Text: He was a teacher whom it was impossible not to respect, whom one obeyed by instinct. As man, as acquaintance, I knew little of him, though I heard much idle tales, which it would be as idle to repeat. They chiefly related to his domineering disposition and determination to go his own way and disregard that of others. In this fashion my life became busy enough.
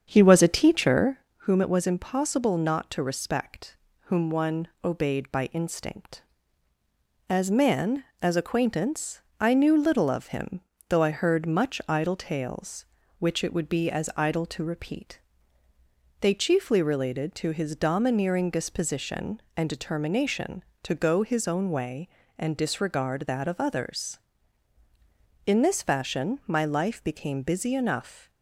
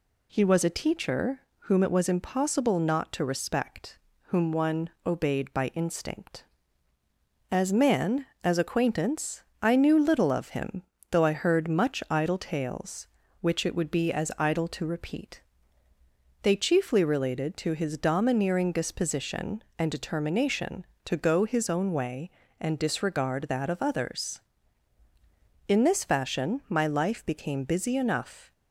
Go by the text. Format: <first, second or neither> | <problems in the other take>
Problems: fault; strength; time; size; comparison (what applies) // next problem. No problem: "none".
second | starts louder than the rest; strong; until 1.3 s; 7.5 dB // pauses between "teacher" and "whom"; slight; at 1.1 s; 0.22 s long; slight in the second